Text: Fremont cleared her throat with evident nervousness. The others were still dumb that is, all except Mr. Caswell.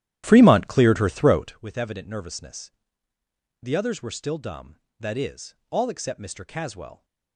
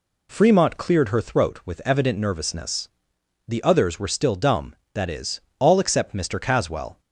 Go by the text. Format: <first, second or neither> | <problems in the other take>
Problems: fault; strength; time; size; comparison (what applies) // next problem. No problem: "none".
second | starts louder than the rest; strong; until 1.7 s; 12 dB